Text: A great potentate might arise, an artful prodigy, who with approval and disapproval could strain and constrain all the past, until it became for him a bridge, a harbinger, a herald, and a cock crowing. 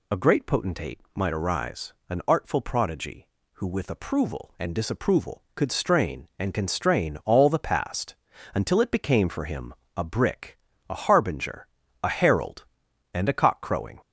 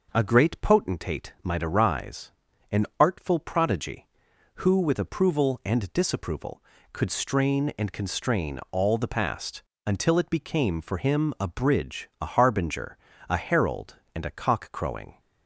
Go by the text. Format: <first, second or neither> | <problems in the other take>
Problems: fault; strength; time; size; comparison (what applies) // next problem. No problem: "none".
second | pauses between "potentate" and "might"; slight; at 0.9 s; 0.16 s long // pauses between "him" and "a"; slight; at 9.7 s; 0.22 s long // says "brick" for "bridge"; at 10.0 s